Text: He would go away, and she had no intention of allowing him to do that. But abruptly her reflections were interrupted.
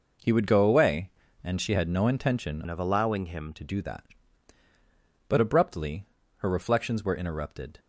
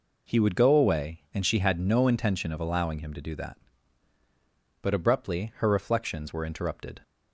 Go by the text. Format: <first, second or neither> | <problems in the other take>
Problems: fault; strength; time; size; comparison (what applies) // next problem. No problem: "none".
second | changes voice from "of" to "him"; from 2.6 to 3.5 s; 0.9 s long // pauses between "abruptly" and "her"; slight; at 6.0 s; 0.32 s long